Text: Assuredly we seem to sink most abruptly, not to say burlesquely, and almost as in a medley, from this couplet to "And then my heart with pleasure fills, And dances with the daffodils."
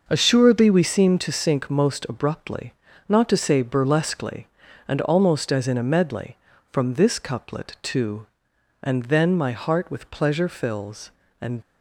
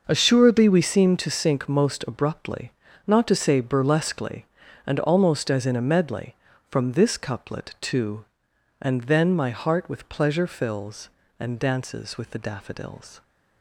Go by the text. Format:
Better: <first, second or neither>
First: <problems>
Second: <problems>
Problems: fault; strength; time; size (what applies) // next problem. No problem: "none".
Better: second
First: stops before "dances with the daffodils"; at 11.6 s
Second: none